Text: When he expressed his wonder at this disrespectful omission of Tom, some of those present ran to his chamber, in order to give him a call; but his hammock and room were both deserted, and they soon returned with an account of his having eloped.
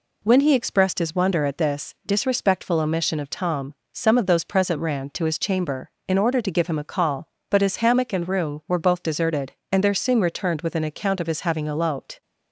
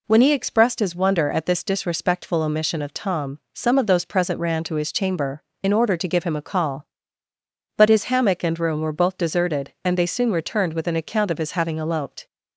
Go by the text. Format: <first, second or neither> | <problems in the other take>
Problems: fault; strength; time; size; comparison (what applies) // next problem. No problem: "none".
second | says "there" for "they"; at 9.8 s